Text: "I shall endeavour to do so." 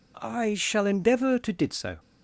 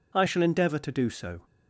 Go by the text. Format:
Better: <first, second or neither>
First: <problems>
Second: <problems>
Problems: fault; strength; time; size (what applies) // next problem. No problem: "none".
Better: second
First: says "did" for "do"; at 1.5 s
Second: none